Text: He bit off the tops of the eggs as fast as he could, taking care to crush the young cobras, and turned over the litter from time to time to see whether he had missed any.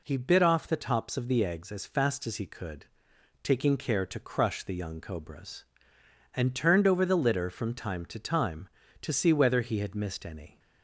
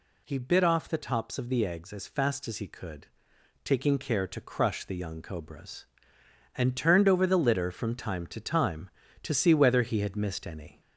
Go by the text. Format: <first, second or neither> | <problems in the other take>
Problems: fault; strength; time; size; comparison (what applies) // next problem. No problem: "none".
first | gets louder; slight; throughout; 3.5 dB